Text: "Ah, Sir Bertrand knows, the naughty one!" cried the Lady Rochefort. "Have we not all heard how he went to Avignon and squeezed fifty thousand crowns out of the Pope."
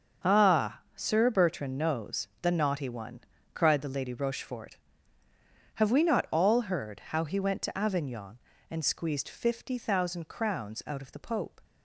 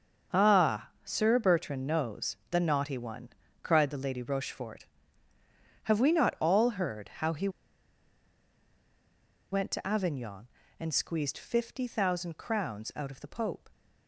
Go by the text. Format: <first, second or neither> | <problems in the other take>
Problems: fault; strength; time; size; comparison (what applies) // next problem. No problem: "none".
first | starts louder than the rest; noticeable; until 1.4 s; 6 dB; noticeable in the first // pauses between "he" and "went"; strong; at 7.4 s; 2.0 s long